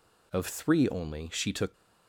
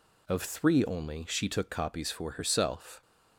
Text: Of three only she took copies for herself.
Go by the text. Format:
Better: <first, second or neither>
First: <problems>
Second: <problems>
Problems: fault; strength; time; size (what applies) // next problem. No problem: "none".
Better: second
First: stops before "copies for herself"; at 1.7 s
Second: none